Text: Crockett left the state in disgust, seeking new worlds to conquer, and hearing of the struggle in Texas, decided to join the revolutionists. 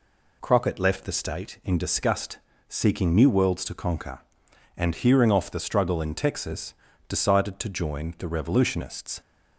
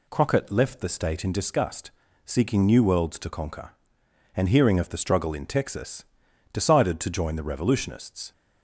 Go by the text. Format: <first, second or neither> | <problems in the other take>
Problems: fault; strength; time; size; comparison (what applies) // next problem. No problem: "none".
second | says "off" for "of"; at 5.3 s